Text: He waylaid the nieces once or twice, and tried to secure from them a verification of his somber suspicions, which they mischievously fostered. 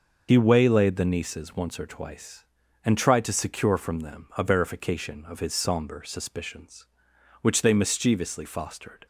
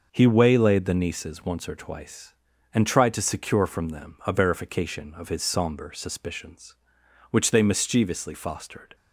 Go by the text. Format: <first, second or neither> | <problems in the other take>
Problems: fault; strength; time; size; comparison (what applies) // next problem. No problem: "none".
second | loses the start of "He"; at 0.2 s; 70 ms